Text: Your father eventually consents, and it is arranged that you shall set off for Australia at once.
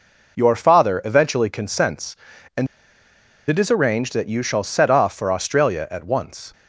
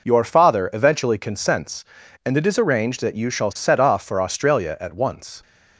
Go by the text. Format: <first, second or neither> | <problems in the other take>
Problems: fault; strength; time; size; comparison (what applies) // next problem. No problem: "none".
second | pauses between "and" and "it"; noticeable; at 2.6 s; 0.81 s long